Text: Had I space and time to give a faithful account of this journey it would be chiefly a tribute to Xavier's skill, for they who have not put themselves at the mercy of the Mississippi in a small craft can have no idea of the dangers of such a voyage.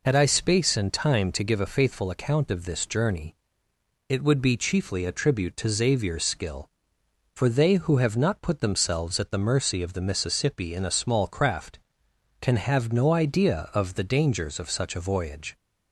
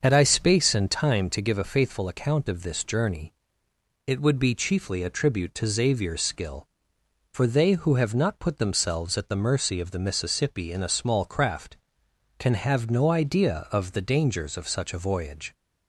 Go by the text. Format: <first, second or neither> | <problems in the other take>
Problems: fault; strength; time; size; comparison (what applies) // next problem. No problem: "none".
first | starts louder than the rest; until 1.0 s; 6.5 dB // pauses between "journey" and "it"; noticeable; at 3.3 s; 0.74 s long; noticeable in the first